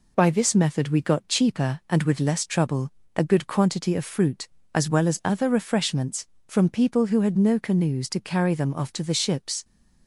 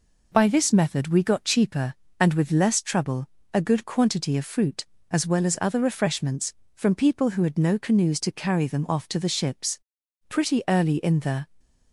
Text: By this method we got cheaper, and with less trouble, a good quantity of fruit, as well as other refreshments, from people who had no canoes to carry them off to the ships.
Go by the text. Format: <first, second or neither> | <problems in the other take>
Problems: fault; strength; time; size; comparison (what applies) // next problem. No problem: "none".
first | goes on to say "Pretty early in the"; noticeable; from 10.3 s on; 1.2 s long